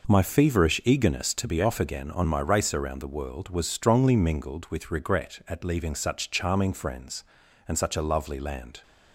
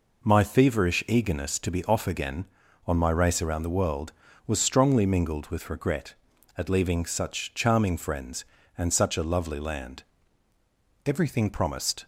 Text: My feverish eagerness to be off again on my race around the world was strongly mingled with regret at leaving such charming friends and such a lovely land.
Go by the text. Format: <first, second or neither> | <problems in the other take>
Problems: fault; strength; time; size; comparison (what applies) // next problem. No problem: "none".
first | goes on to say "Everything promised"; noticeable; from 11.0 s on; 0.98 s long